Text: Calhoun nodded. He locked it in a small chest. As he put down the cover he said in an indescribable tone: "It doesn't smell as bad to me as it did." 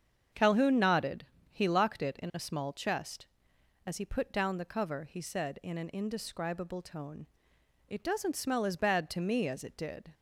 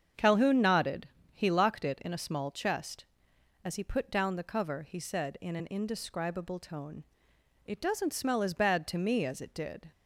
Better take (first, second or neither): neither